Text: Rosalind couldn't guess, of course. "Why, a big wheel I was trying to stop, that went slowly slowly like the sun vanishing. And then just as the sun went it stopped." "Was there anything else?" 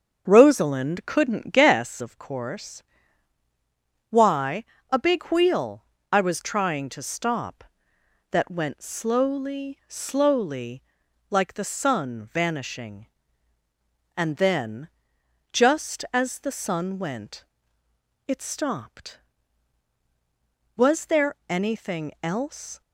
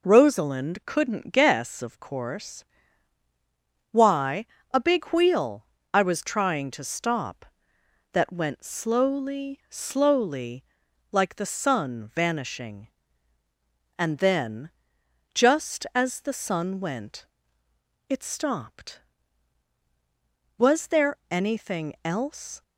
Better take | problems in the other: second | starts louder than the rest; until 1.9 s; 7 dB // pauses between "wheel" and "I"; slight; at 5.8 s; 0.26 s long; slight in the second // pauses between "slowly" and "like"; noticeable; at 10.8 s; 0.48 s long; noticeable in the second // pauses between "then" and "just"; noticeable; at 14.8 s; 0.64 s long; noticeable in the second // pauses between "went" and "it"; noticeable; at 17.4 s; 0.82 s long; noticeable in the second // pauses between "there" and "anything"; slight; at 21.3 s; 0.16 s long; slight in the second

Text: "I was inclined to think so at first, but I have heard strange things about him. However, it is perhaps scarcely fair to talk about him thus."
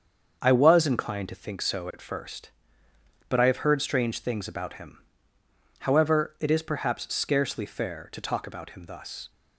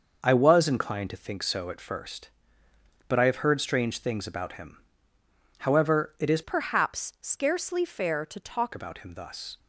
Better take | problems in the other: first | starts louder than the rest; noticeable; until 1.2 s; 6 dB; also in the first // changes voice from "perhaps" to "talk"; from 6.4 to 8.7 s; 2.3 s long

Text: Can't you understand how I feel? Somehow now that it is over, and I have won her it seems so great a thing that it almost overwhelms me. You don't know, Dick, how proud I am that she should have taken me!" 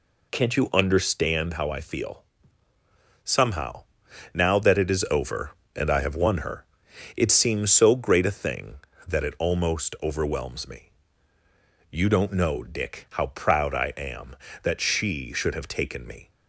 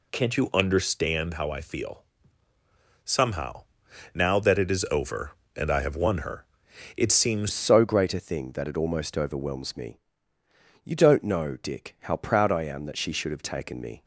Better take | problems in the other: first | pauses between "Somehow" and "now"; noticeable; at 3.6 s; 0.50 s long; noticeable in the first // pauses between "her" and "it"; noticeable; at 6.4 s; 0.50 s long; noticeable in the first // changes voice at "so"; from 7.5 s on; 6.5 s long

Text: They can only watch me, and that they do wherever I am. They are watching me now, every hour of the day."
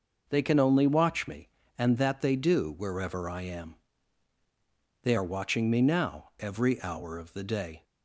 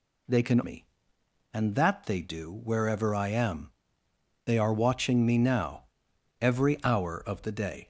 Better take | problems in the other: first | skips "only watch"; at 0.6 s

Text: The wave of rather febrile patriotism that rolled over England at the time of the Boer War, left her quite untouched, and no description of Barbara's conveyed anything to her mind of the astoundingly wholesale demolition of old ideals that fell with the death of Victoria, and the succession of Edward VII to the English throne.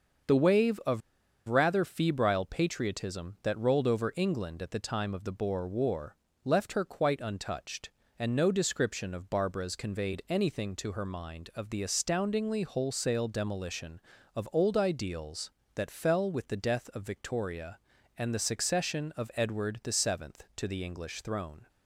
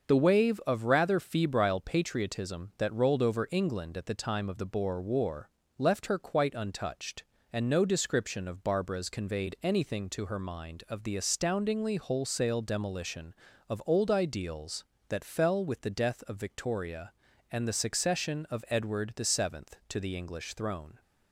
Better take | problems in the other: second | starts louder than the rest; until 1.8 s; 6.5 dB; also in the second // pauses between "of" and "rather"; noticeable; at 1.0 s; 0.47 s long

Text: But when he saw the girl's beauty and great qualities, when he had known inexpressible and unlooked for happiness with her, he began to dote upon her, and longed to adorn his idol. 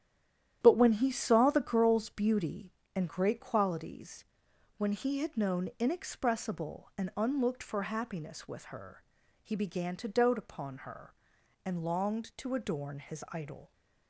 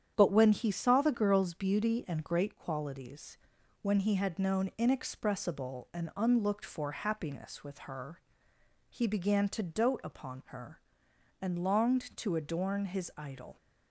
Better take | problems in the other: second | stays silent before the first word; slight; until 0.6 s; 0.6 s long // starts louder than the rest; strong; until 1.6 s; 11 dB; strong in the second

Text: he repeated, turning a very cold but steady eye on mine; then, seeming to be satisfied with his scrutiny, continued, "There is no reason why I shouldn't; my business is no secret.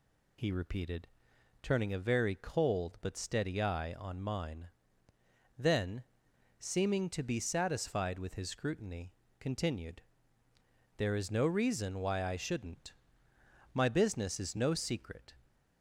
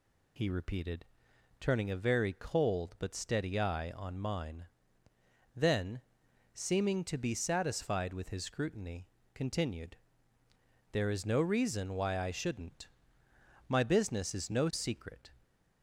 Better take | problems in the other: neither | none

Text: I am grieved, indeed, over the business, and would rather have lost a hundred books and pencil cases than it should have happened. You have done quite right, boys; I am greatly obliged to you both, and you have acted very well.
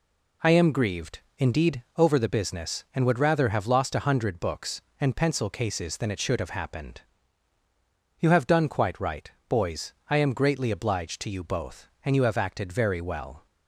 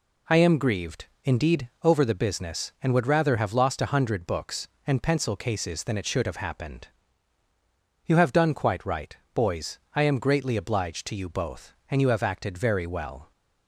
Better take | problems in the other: neither | none

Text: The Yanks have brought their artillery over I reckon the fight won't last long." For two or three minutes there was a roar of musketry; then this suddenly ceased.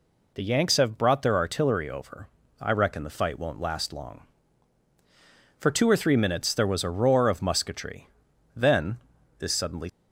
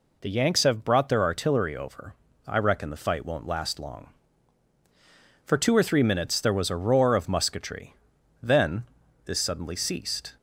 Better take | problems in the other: second | pauses between "over" and "I"; slight; at 2.2 s; 0.34 s long; slight in the second // pauses between "then" and "this"; at 8.9 s; 0.40 s long; also in the second // stops before "ceased"; at 9.8 s

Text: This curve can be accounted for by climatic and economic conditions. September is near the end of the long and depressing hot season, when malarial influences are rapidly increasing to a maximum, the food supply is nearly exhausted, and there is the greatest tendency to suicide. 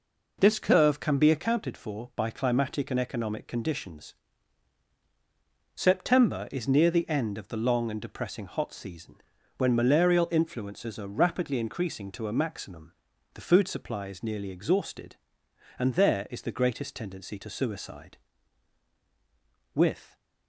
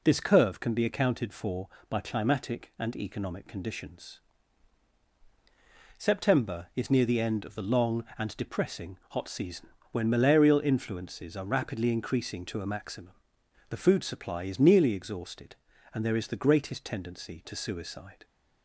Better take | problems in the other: second | goes on to say "With"; slight; from 19.7 s on; 0.42 s long

